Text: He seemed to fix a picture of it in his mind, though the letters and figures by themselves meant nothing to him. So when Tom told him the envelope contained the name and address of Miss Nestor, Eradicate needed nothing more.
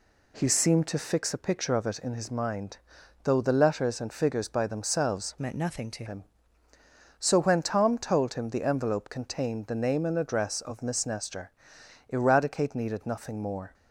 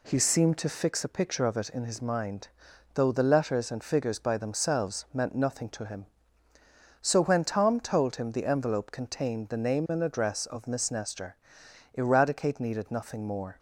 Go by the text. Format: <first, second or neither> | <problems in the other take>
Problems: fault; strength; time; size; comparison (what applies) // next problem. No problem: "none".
second | changes voice from "meant" to "to"; from 5.4 to 6.0 s; 0.6 s long